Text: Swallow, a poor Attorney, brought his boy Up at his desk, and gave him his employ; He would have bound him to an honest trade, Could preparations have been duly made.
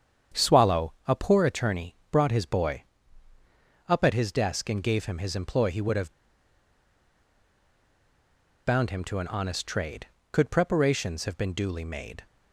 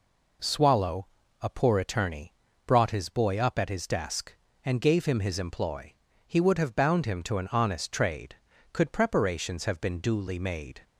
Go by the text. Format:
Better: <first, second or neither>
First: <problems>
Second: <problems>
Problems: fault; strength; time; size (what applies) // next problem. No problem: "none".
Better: second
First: starts louder than the rest; strong; until 1.4 s; 8 dB // pauses between "boy" and "Up"; at 2.8 s; 1.0 s long // pauses between "have" and "bound"; strong; at 6.1 s; 2.5 s long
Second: none